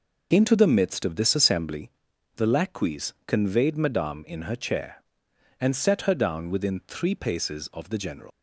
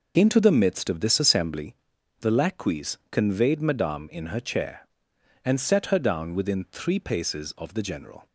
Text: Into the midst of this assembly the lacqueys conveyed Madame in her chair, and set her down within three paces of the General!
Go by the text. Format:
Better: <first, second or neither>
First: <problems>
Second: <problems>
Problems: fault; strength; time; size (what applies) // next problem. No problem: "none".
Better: second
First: pauses between "assembly" and "the"; noticeable; at 1.8 s; 0.48 s long // leaves "General" unfinished; at 8.3 s; 115 ms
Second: pauses between "assembly" and "the"; noticeable; at 1.7 s; 0.48 s long